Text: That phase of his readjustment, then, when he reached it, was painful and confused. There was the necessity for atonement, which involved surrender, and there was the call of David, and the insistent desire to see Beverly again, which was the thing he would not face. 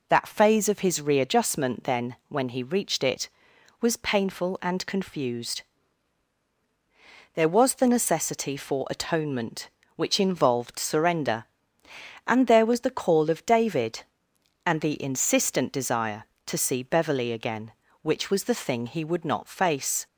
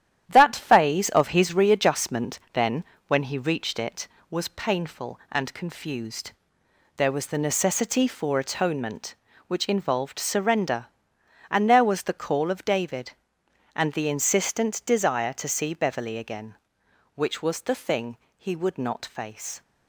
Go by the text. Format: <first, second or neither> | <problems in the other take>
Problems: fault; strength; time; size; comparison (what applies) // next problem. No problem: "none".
first | gets quieter; noticeable; throughout; 6 dB // pauses between "thing" and "he"; slight; at 18.1 s; 0.18 s long